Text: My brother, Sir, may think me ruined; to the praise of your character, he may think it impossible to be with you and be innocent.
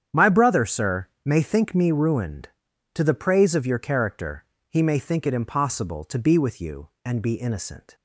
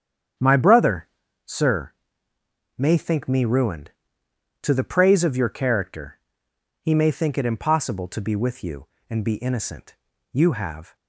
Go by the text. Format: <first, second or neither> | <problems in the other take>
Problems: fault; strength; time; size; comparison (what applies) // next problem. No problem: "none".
first | starts louder than the rest; strong; until 1.7 s; 8.5 dB; strong in the first // goes on to say "You have"; noticeable; from 10.3 s on; 0.62 s long